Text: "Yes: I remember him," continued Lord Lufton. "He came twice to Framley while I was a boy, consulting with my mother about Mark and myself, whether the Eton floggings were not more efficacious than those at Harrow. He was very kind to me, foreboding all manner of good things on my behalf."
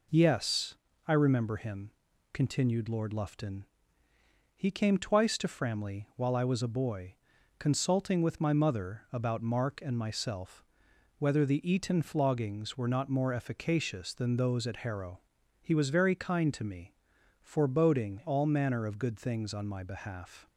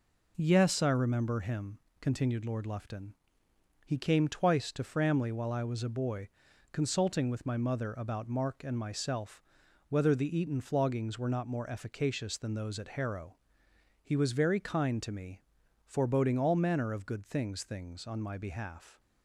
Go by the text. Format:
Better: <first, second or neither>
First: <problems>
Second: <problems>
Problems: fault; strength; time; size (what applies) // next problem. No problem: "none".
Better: first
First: none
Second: says "things" twice; at 17.6 s